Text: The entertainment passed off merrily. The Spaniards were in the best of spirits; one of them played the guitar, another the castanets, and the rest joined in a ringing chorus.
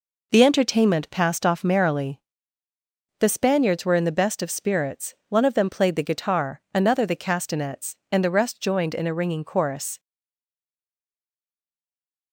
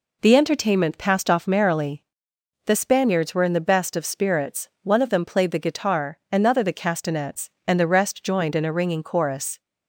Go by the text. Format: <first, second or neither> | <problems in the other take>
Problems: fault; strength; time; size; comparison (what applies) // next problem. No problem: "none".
second | stays silent after the last word; from 9.9 s on; 2.4 s long